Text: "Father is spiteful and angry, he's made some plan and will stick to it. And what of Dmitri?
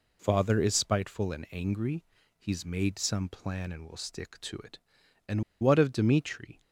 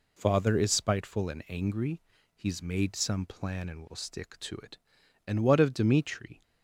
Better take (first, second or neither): second